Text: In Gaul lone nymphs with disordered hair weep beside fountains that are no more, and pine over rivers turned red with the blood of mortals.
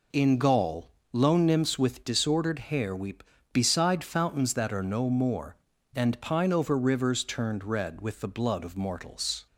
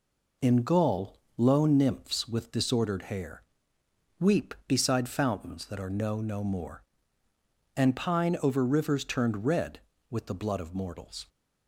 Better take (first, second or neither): first